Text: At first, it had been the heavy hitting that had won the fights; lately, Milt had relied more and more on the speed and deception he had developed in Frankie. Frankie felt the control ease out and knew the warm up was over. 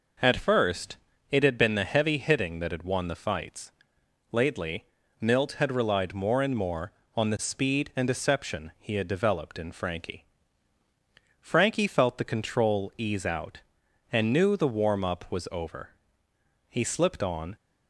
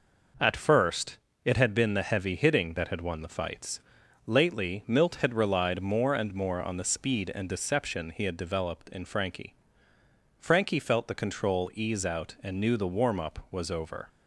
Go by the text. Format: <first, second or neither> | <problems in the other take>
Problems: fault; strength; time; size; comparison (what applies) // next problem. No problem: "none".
second | goes on to say "He slipped on"; noticeable; from 16.6 s on; 0.88 s long